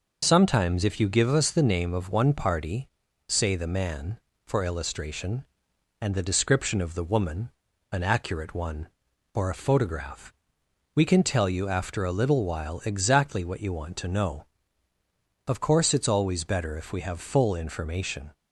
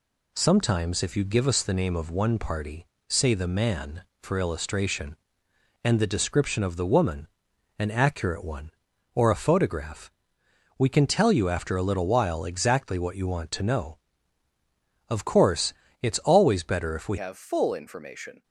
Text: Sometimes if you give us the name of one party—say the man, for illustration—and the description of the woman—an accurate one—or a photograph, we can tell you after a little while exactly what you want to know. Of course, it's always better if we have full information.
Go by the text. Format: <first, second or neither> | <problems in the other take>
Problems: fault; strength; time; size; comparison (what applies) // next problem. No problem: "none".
first | changes voice at "have"; from 17.1 s on; 1.3 s long